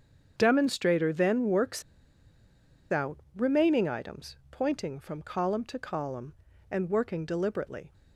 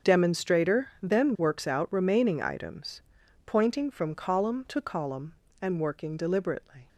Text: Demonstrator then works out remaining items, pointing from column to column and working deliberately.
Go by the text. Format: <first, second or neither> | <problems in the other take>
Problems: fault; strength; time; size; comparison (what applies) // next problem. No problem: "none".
second | starts louder than the rest; strong; until 1.3 s; 7.5 dB; also in the second // pauses between "works" and "out"; at 1.8 s; 1.0 s long // pauses between "out" and "remaining"; slight; at 3.1 s; 0.18 s long